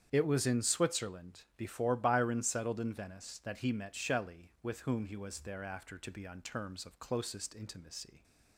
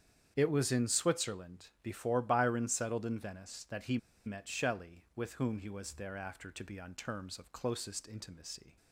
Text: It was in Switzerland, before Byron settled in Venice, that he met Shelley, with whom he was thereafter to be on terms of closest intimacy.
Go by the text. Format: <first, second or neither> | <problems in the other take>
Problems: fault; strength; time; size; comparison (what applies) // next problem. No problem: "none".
first | starts louder than the rest; strong; until 1.3 s; 8.5 dB; strong in the first // pauses between "he" and "met"; slight; at 3.9 s; 0.27 s long